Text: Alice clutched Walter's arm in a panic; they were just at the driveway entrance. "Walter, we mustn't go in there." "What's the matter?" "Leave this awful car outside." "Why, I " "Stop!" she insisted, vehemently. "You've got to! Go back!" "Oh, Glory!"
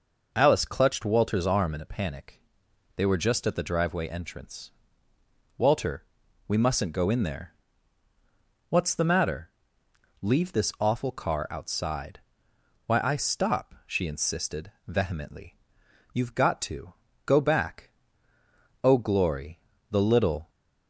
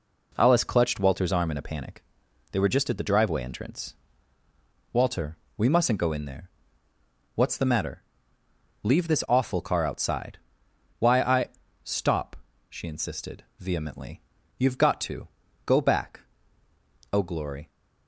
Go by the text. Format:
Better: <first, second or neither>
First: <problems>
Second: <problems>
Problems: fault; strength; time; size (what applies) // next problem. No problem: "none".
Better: second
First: goes on to say "The little"; from 19.9 s on; 0.58 s long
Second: none